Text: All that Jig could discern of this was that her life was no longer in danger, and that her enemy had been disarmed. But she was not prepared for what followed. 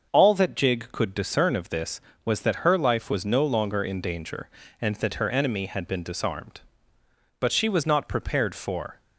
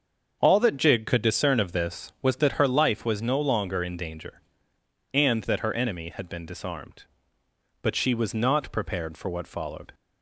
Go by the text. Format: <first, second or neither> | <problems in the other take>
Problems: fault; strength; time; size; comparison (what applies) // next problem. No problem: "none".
second | starts louder than the rest; until 1.1 s; 6 dB; also in the second // stops before "what followed"; at 8.9 s